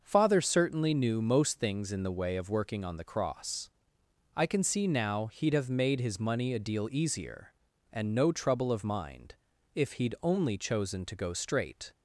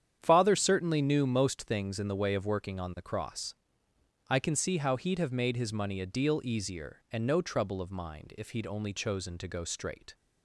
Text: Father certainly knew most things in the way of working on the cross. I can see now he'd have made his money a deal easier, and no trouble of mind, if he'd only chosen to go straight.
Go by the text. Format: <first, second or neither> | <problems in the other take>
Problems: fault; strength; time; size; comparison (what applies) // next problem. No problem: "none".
first | starts louder than the rest; strong; until 1.2 s; 9 dB; noticeable in the first // says "how" for "now"; at 4.7 s